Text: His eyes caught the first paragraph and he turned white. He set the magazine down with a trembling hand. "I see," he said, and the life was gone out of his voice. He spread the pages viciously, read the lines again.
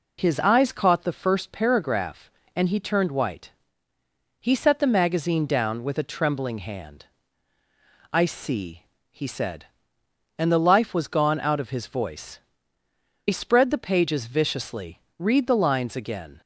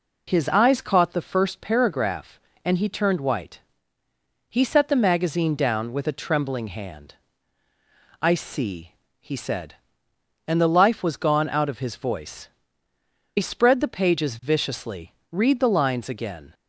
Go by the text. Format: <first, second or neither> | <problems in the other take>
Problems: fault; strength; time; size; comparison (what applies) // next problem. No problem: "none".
neither | none